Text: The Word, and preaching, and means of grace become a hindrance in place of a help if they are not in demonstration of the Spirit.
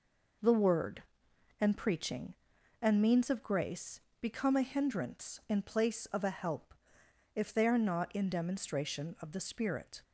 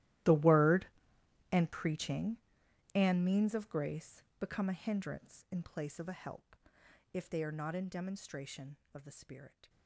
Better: first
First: pauses between "grace" and "become"; slight; at 4.0 s; 0.20 s long // pauses between "help" and "if"; noticeable; at 6.7 s; 0.60 s long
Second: gets quieter; strong; throughout; 21.5 dB // pauses between "grace" and "become"; slight; at 4.2 s; 0.16 s long // pauses between "help" and "if"; noticeable; at 6.5 s; 0.56 s long

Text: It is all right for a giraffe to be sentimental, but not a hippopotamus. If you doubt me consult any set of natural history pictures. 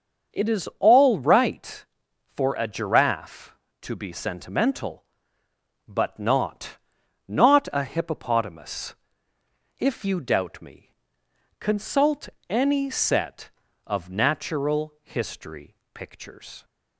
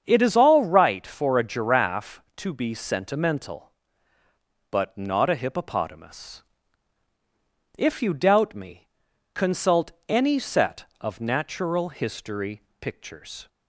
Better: second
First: starts louder than the rest; until 1.4 s; 6.5 dB // says "not" twice; at 7.2 s // pauses between "me" and "consult"; noticeable; at 10.9 s; 0.64 s long // pauses between "consult" and "any"; slight; at 12.2 s; 0.20 s long // pauses between "history" and "pictures"; slight; at 15.7 s; 0.18 s long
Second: starts louder than the rest; strong; until 1.0 s; 7.5 dB // pauses between "me" and "consult"; at 8.8 s; 0.44 s long // pauses between "consult" and "any"; slight; at 9.9 s; 0.16 s long // pauses between "history" and "pictures"; slight; at 12.5 s; 0.22 s long

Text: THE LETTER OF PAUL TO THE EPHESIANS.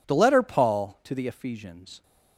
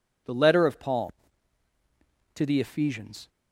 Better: second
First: skips "OF"; at 0.4 s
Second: none

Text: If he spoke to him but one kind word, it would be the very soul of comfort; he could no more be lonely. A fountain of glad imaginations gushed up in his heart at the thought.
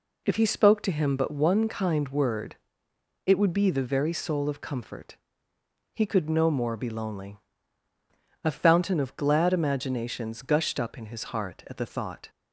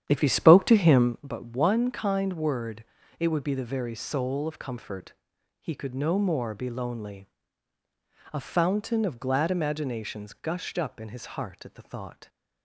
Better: first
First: none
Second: starts louder than the rest; strong; until 1.2 s; 9.5 dB

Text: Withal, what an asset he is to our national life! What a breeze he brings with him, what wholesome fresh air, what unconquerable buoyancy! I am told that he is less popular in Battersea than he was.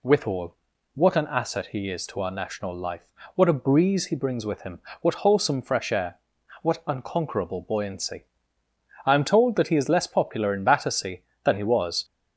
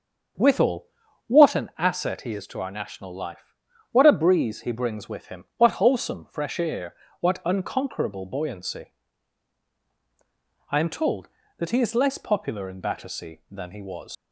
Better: first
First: none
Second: starts louder than the rest; until 1.8 s; 7 dB // leaves "was" unfinished; at 14.1 s; 110 ms

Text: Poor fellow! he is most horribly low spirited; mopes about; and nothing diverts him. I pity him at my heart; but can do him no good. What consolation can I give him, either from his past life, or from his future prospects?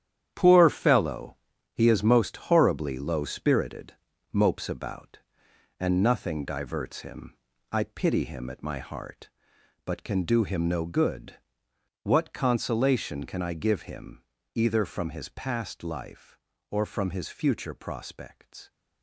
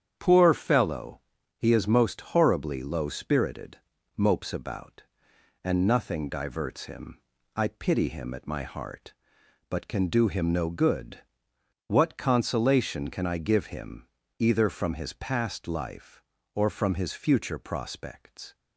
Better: second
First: gets quieter; strong; throughout; 9.5 dB // starts louder than the rest; strong; until 1.3 s; 10 dB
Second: starts louder than the rest; strong; until 1.1 s; 8.5 dB

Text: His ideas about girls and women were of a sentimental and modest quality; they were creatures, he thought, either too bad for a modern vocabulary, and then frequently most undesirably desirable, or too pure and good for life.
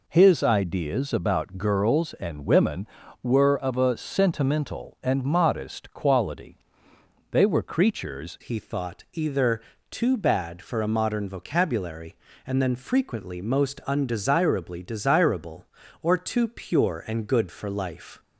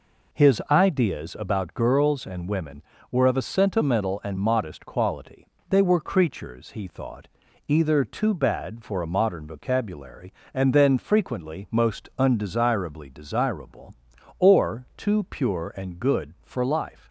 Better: second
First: changes voice at "he"; from 8.4 s on; 9.7 s long // pauses between "either" and "too"; slight; at 9.5 s; 0.30 s long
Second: none

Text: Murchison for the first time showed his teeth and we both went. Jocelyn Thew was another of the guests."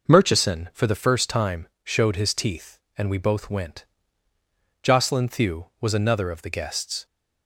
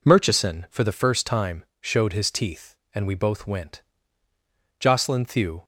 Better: first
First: pauses between "time" and "showed"; slight; at 1.6 s; 0.16 s long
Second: pauses between "time" and "showed"; slight; at 1.6 s; 0.16 s long // stops before "was another of the guests"; at 5.6 s

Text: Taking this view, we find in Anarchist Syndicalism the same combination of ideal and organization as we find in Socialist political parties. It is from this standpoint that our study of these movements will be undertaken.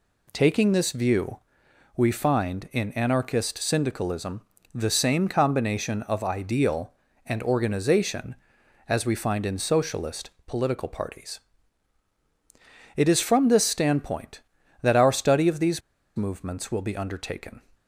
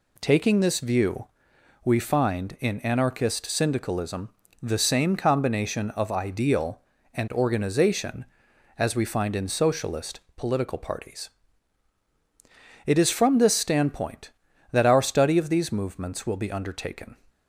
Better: second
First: pauses between "Syndicalism" and "the"; slight; at 4.4 s; 0.32 s long // pauses between "Socialist" and "political"; slight; at 10.3 s; 0.16 s long // pauses between "these" and "movements"; at 15.8 s; 0.36 s long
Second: pauses between "Syndicalism" and "the"; slight; at 4.2 s; 0.32 s long // pauses between "Socialist" and "political"; slight; at 10.2 s; 0.16 s long

